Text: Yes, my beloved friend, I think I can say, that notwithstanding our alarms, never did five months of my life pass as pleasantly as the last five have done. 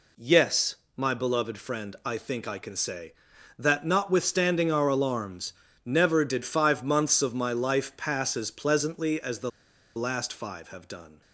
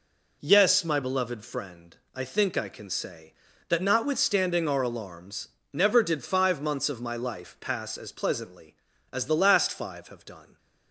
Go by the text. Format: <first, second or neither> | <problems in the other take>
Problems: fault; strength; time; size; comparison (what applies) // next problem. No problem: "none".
second | pauses between "the" and "last"; noticeable; at 9.5 s; 0.46 s long